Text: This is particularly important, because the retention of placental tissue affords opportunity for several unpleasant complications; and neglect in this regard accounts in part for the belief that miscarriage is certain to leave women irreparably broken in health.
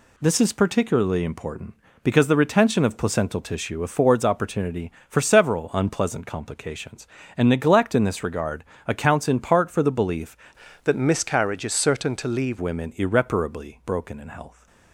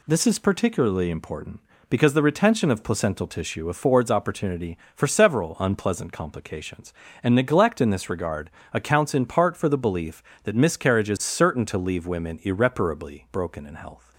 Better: second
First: pauses between "regard" and "accounts"; slight; at 8.6 s; 0.22 s long // changes voice from "that" to "leave"; from 10.8 to 12.5 s; 1.7 s long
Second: pauses between "regard" and "accounts"; slight; at 8.5 s; 0.22 s long

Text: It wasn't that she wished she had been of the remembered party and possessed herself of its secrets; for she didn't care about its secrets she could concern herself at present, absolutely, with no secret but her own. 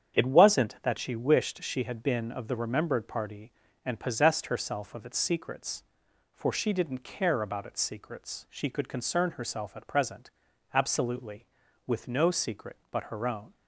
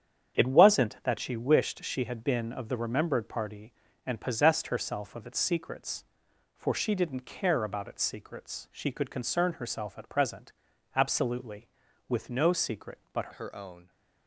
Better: first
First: starts louder than the rest; strong; until 1.2 s; 8.5 dB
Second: starts louder than the rest; strong; until 1.4 s; 8.5 dB // changes voice at "her"; from 13.3 s on; 0.5 s long

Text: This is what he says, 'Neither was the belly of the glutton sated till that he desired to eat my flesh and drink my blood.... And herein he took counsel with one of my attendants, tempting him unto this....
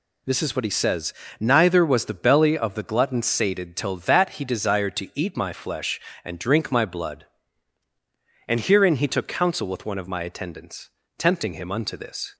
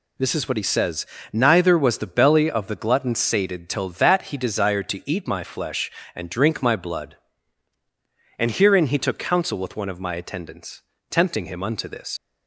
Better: first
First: none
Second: leaves "this" unfinished; at 12.1 s; 95 ms

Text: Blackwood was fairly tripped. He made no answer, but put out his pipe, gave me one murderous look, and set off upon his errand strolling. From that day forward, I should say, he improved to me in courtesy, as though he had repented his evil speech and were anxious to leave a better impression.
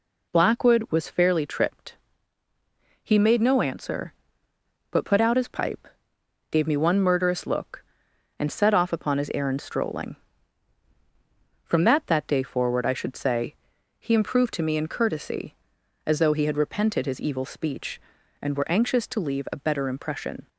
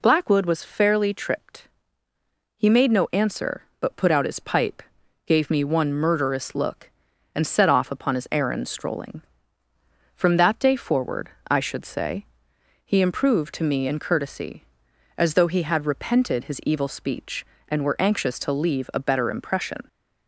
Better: second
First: says "that" twice; at 12.0 s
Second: none

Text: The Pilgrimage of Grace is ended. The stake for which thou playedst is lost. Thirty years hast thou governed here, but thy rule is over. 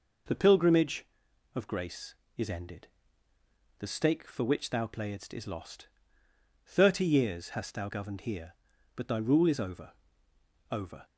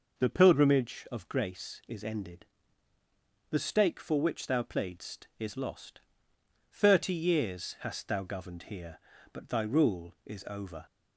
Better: second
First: says "over" twice; at 10.7 s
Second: none

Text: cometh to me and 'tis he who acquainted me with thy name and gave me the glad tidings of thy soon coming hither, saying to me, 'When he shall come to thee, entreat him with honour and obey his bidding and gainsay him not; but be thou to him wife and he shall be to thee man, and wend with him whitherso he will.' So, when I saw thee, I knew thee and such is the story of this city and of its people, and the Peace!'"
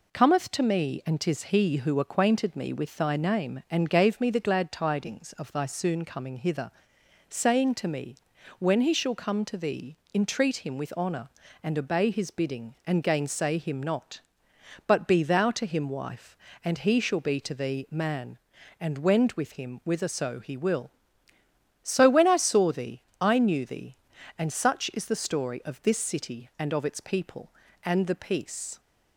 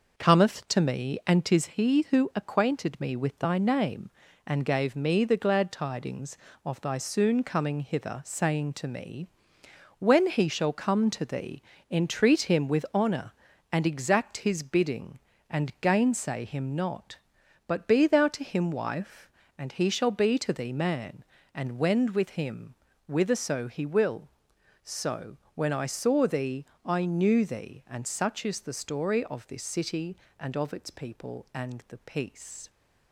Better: first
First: none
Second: says "exact" for "obey"; at 13.8 s // pauses between "him" and "whitherso"; slight; at 22.7 s; 0.36 s long

